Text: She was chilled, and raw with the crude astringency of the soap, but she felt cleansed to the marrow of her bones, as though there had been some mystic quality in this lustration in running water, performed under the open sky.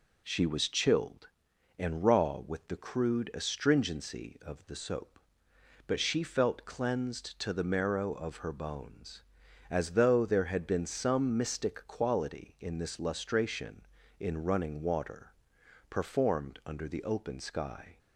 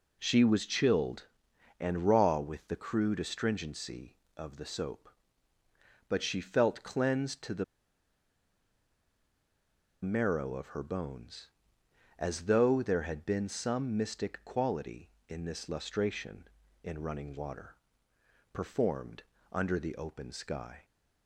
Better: first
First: none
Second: pauses between "the" and "marrow"; strong; at 7.6 s; 2.3 s long // pauses between "performed" and "under"; slight; at 19.2 s; 0.32 s long

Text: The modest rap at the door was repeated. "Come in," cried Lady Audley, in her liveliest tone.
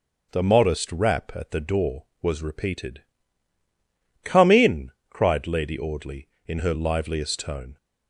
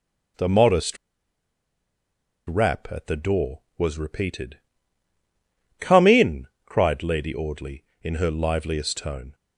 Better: first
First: starts louder than the rest; noticeable; until 1.3 s; 6 dB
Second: starts louder than the rest; noticeable; until 2.8 s; 6 dB // pauses between "modest" and "rap"; strong; at 0.9 s; 1.5 s long

